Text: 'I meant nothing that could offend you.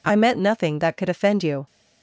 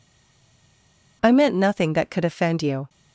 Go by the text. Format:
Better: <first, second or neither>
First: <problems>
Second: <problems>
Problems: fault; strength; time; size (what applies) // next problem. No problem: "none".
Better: first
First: none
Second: stays silent before the first word; noticeable; until 1.2 s; 1.2 s long